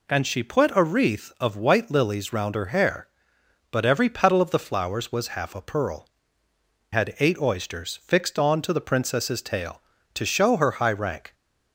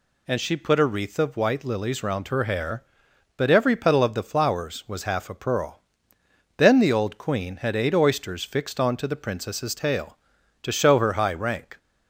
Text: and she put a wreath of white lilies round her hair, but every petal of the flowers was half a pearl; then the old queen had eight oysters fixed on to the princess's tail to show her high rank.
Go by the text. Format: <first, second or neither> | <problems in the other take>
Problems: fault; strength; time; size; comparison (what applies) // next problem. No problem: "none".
second | skips "then the old queen"; at 6.4 s